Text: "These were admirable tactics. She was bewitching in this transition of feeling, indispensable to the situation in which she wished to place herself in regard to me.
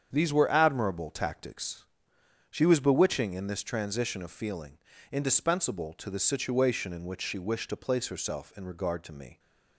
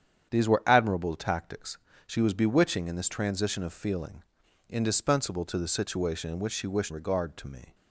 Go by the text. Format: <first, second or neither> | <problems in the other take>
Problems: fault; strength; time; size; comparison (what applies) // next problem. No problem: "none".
first | starts louder than the rest; strong; until 1.3 s; 8.5 dB; strong in the first // skips "to place herself in"; at 6.9 s